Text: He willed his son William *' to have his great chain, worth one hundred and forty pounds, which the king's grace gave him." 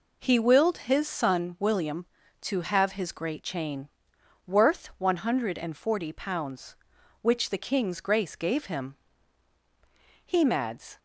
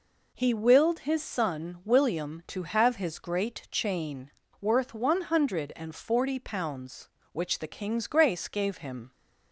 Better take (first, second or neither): second